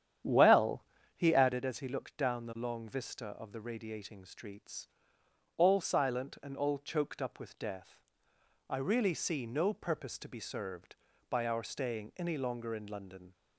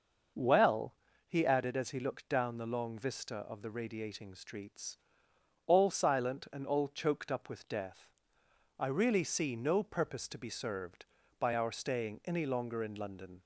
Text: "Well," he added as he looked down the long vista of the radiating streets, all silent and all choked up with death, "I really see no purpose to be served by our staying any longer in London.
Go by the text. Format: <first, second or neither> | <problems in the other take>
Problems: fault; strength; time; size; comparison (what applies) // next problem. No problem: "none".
second | starts louder than the rest; strong; until 1.6 s; 9.5 dB